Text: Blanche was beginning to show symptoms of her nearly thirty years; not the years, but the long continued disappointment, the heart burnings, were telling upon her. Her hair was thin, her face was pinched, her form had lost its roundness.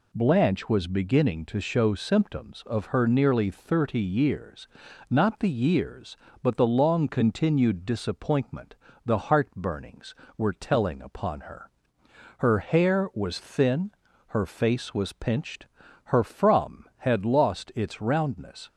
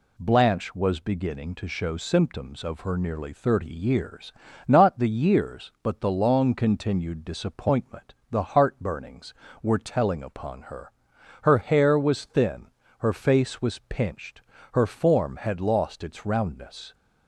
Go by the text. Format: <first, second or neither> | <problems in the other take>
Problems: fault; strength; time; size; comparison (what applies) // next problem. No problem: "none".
second | says "from" for "form"; at 16.2 s